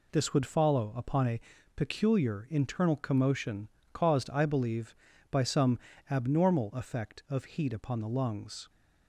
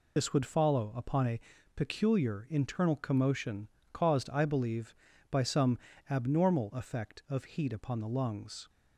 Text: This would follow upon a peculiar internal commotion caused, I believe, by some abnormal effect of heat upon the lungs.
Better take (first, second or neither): first